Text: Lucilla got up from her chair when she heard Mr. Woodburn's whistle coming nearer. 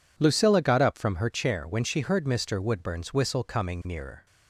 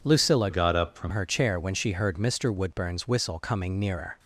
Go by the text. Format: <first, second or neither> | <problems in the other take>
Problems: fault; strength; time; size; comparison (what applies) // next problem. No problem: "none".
first | changes voice from "got" to "from"; from 0.4 to 1.1 s; 0.7 s long